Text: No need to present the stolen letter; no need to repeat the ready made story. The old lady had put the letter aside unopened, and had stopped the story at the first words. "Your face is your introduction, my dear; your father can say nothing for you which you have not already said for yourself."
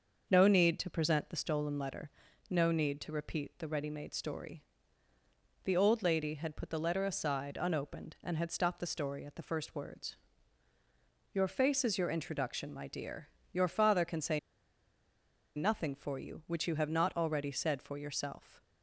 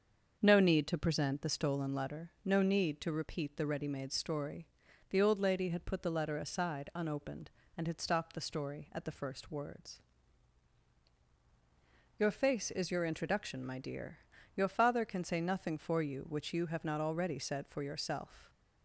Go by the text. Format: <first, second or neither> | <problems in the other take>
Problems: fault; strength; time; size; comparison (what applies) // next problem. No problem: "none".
second | starts louder than the rest; until 1.3 s; 6 dB; also in the second // pauses between "say" and "nothing"; at 14.3 s; 1.1 s long